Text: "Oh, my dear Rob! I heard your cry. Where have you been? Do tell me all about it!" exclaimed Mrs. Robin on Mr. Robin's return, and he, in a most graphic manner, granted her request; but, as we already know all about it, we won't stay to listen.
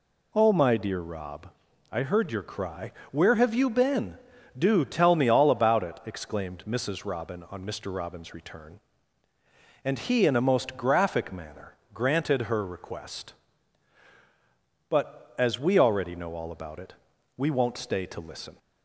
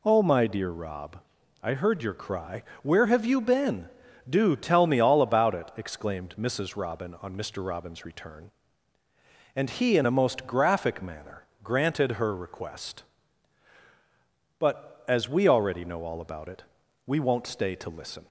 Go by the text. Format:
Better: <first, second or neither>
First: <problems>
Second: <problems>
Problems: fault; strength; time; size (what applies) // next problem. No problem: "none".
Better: neither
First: none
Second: none